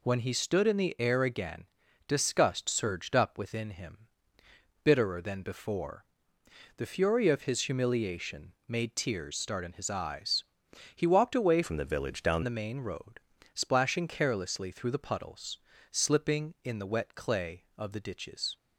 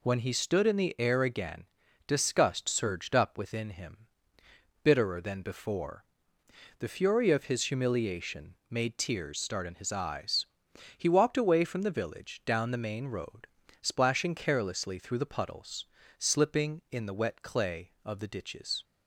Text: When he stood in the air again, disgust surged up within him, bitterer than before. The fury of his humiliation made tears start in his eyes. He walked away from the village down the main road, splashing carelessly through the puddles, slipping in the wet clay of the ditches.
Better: second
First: pauses between "humiliation" and "made"; slight; at 8.5 s; 0.16 s long // changes voice from "from" to "down"; from 11.6 to 12.4 s; 0.8 s long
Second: pauses between "humiliation" and "made"; slight; at 8.5 s; 0.16 s long

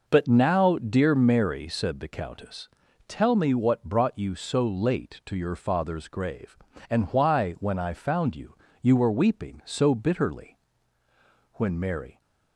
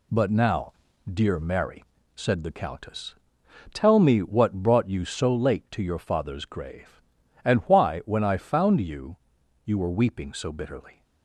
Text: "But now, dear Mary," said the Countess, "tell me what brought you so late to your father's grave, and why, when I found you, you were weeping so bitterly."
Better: second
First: goes on to say "When Mary"; noticeable; from 11.5 s on; 0.66 s long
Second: none

